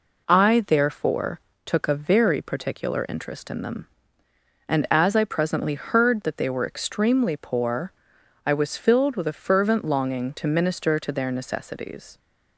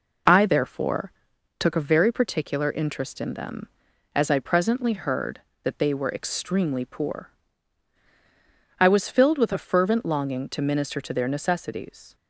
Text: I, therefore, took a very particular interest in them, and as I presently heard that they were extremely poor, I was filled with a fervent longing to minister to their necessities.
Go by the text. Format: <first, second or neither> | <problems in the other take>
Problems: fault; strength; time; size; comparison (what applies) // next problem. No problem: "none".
first | skips "and"; at 3.9 s